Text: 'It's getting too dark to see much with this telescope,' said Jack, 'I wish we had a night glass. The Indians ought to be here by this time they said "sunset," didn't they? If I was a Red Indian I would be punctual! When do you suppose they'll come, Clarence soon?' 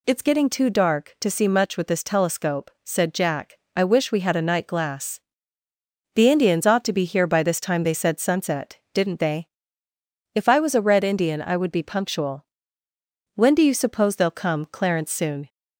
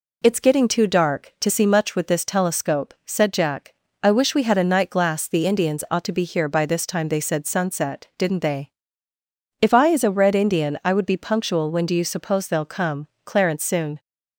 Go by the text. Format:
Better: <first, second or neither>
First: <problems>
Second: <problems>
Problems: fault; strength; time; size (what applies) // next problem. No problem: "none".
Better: first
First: none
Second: says "is" for "was"; at 9.8 s